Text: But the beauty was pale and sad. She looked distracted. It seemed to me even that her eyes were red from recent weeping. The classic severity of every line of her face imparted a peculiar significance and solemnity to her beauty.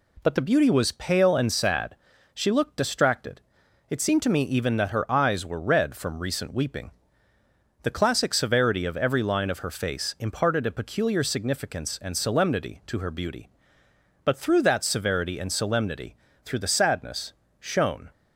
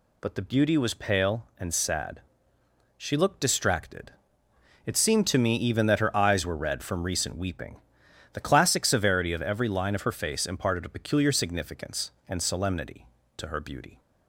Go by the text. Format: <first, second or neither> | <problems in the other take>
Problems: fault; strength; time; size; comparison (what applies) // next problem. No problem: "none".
second | goes on to say "But through that severity and solemnity through the sadness shone"; strong; from 14.2 s on; 3.8 s long